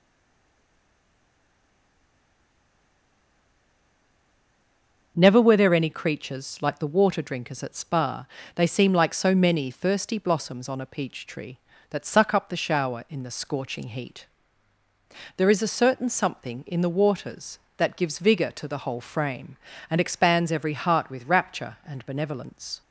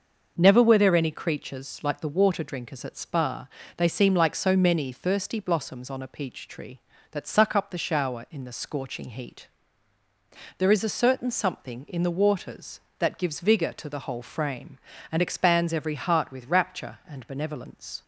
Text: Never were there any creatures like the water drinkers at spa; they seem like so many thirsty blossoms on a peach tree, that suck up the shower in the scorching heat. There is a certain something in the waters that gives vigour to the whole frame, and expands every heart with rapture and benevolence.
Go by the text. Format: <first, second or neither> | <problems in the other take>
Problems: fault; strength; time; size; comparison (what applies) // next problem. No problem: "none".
second | stays silent before the first word; strong; until 5.1 s; 5.1 s long // starts louder than the rest; noticeable; until 6.1 s; 6 dB; noticeable in the second